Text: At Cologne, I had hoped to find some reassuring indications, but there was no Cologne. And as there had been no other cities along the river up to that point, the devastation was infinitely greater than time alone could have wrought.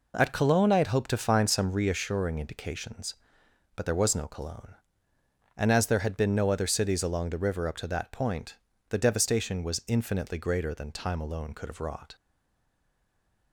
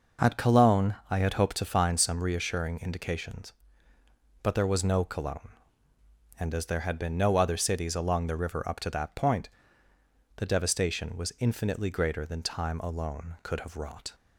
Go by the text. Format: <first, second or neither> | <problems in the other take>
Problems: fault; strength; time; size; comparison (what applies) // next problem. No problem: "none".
second | stays silent after the last word; noticeable; from 12.1 s on; 1.4 s long